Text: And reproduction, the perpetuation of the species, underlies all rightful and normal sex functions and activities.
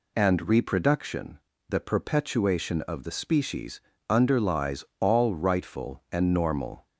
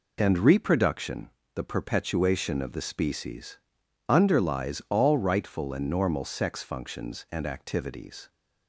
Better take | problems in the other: second | pauses between "underlies" and "all"; slight; at 4.8 s; 0.16 s long // stops before "sex functions and activities"; at 6.8 s

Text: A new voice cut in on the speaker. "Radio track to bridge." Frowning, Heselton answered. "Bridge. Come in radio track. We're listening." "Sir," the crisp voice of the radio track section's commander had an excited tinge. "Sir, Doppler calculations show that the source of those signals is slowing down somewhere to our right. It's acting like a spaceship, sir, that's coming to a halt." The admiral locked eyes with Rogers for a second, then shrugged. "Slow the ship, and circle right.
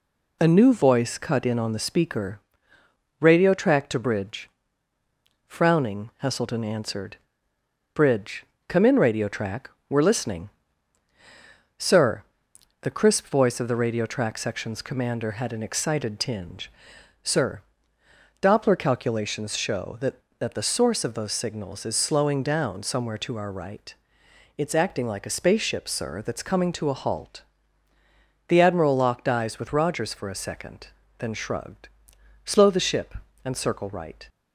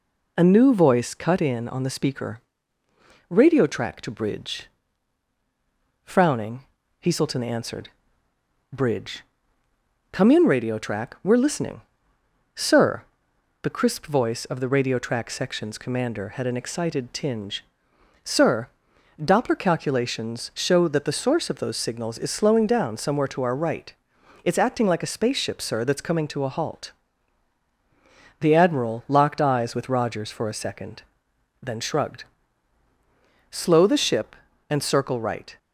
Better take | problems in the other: second | says "that" twice; at 20.3 s

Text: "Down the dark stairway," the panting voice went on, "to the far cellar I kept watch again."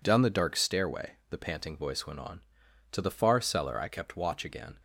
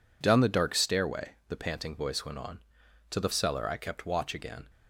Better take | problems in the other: first | skips "far"; at 3.3 s

